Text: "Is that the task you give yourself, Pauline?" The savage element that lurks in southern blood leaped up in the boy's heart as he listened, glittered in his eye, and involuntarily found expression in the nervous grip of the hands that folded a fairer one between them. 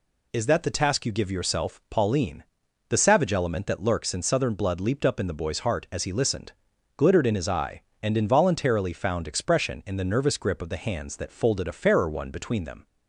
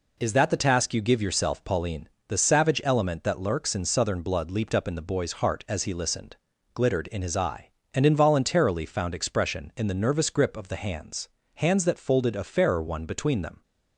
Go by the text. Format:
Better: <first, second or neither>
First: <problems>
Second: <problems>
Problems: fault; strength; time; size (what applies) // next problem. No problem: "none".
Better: first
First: none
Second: says "hands" twice; at 11.5 s